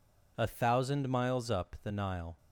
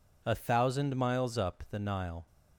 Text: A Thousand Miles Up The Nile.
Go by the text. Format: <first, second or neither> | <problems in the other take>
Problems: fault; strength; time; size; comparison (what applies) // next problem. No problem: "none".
neither | none